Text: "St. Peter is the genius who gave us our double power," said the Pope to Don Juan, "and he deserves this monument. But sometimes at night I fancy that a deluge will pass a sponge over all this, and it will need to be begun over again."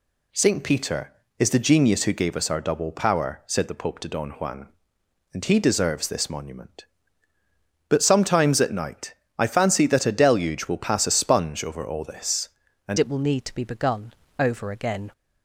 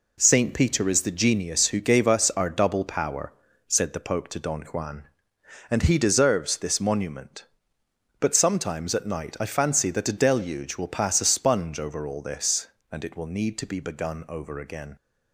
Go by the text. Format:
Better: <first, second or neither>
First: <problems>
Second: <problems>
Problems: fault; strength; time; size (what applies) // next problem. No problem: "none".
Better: second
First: pauses between "night" and "I"; slight; at 9.1 s; 0.22 s long // changes voice at "it"; from 12.9 s on; 2.2 s long // pauses between "begun" and "over"; slight; at 14.1 s; 0.26 s long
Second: none